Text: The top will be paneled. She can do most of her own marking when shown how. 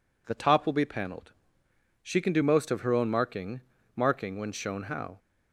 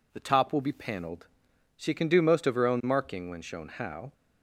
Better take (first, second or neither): second